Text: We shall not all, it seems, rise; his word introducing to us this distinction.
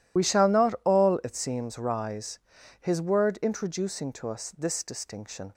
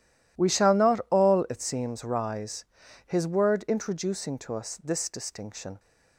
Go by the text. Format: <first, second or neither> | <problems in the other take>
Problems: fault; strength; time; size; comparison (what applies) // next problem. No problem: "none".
second | loses the start of "We"; at 0.1 s; 40 ms